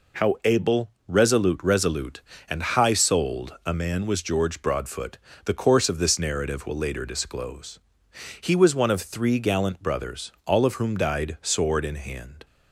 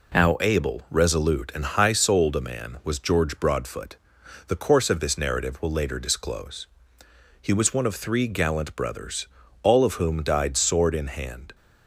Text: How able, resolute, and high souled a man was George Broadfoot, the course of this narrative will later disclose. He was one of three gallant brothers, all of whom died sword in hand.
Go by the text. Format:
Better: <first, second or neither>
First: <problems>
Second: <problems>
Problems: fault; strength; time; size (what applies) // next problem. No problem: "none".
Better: second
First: says "resolute" twice; at 1.6 s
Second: none